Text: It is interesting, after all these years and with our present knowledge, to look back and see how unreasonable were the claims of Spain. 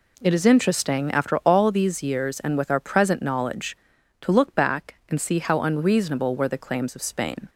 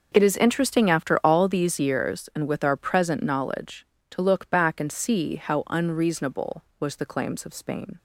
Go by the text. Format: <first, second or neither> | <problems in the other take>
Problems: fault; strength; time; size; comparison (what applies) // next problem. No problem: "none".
first | says "was" for "were"; at 6.7 s